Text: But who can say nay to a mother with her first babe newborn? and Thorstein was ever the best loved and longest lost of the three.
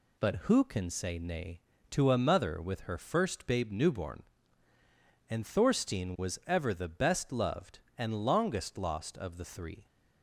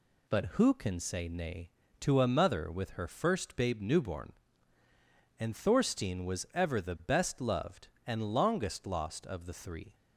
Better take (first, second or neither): neither